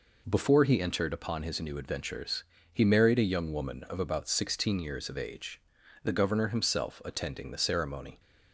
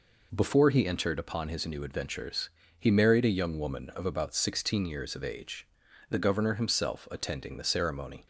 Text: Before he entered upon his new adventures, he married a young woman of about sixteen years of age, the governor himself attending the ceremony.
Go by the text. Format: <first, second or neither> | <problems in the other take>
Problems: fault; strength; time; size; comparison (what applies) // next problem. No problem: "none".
neither | none